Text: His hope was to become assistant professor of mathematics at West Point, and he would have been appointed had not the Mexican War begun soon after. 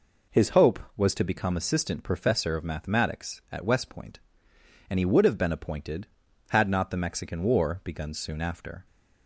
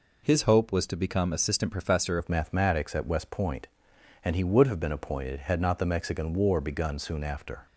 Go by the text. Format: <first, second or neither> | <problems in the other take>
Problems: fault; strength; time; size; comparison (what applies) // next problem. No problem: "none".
first | changes voice at "of"; from 2.1 s on; 5.5 s long